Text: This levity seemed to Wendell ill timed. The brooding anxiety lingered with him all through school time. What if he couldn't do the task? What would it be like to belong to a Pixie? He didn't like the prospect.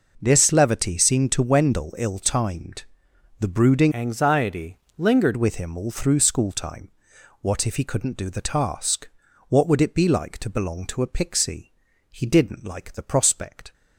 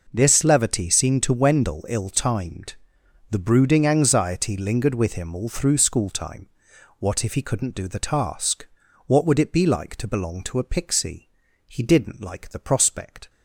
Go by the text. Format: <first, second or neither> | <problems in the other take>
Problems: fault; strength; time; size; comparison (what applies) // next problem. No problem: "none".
second | changes voice from "anxiety" to "lingered"; from 3.9 to 5.3 s; 1.4 s long // pauses between "anxiety" and "lingered"; slight; at 4.7 s; 0.20 s long